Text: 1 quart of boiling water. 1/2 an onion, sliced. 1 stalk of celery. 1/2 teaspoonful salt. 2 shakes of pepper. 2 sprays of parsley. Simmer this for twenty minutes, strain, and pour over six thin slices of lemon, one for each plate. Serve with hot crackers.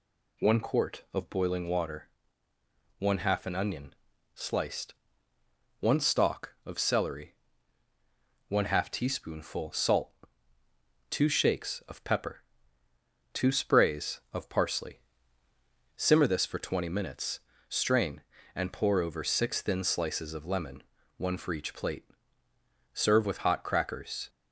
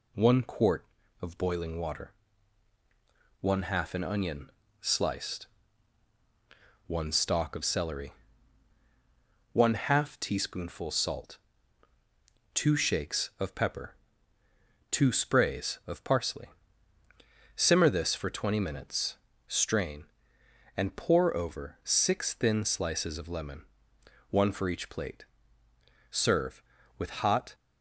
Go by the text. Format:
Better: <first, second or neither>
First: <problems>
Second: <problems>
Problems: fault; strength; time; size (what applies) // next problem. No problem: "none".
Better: first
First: none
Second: stops before "crackers"; at 27.5 s